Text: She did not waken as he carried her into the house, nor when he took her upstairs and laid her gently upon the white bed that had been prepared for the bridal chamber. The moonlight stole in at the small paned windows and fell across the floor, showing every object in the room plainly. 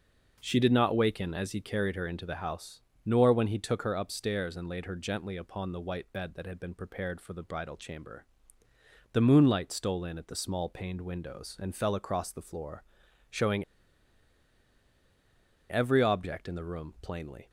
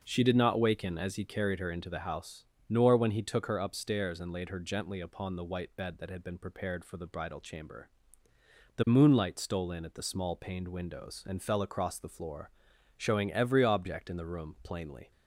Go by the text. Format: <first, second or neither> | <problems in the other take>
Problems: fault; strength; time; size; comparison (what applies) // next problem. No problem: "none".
second | pauses between "showing" and "every"; strong; at 13.6 s; 2.0 s long